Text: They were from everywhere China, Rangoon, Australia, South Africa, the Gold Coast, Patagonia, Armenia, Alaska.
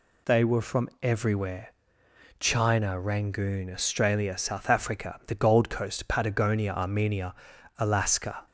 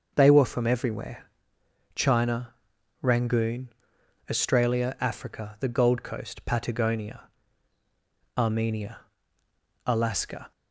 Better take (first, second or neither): first